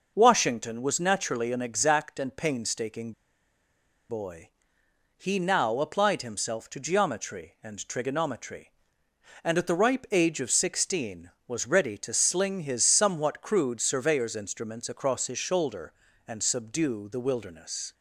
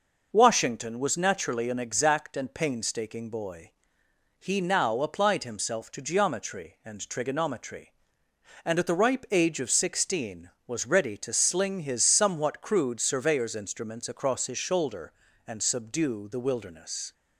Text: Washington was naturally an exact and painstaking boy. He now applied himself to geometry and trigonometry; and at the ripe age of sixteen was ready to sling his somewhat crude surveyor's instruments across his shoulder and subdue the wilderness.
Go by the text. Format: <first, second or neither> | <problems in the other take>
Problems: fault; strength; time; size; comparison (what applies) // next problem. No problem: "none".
second | pauses between "painstaking" and "boy"; noticeable; at 3.1 s; 0.98 s long